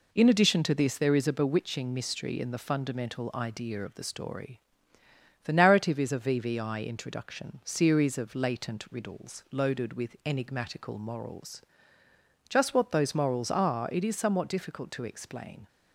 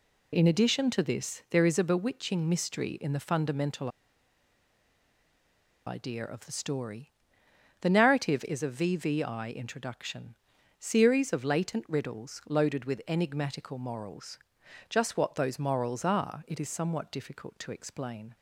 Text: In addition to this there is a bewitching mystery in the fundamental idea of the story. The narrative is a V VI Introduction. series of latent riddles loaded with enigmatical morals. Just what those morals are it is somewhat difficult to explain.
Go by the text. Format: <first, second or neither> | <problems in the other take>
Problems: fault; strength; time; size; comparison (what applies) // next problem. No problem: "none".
first | pauses between "fundamental" and "idea"; strong; at 3.8 s; 1.9 s long